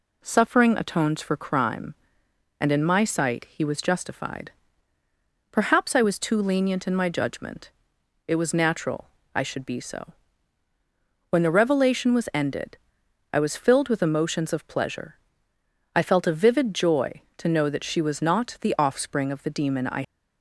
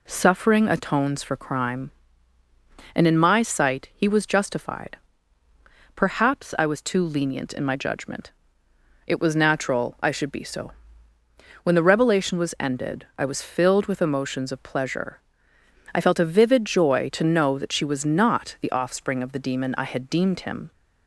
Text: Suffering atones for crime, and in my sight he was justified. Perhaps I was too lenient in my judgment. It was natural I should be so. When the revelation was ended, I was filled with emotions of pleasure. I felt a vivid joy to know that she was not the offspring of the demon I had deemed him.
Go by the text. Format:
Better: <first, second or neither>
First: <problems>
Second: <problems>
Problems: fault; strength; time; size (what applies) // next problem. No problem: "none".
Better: second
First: pauses between "natural" and "I"; slight; at 9.0 s; 0.26 s long // stops before "had deemed him"; at 20.0 s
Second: none